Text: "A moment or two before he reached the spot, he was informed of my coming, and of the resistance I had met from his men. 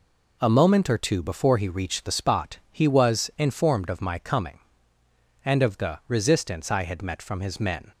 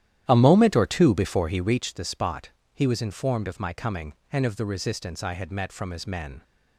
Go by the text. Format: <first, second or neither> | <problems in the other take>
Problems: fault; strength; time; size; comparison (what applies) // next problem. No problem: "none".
first | starts louder than the rest; strong; until 1.8 s; 11.5 dB